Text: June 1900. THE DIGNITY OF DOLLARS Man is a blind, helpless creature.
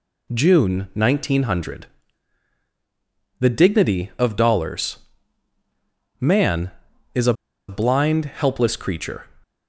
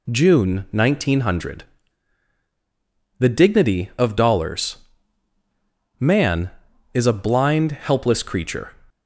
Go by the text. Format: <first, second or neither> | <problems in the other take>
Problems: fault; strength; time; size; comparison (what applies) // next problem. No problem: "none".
second | pauses between "DOLLARS" and "Man"; at 4.9 s; 1.2 s long; also in the second // pauses between "a" and "blind"; slight; at 7.3 s; 0.35 s long